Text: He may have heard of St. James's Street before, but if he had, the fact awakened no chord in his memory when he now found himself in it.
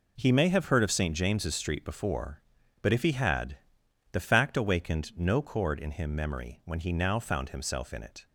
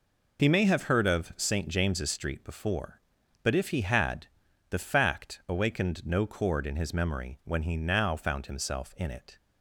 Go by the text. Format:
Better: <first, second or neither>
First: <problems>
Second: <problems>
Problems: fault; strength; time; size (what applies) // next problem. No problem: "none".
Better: second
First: says "him" for "his"; at 5.9 s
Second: none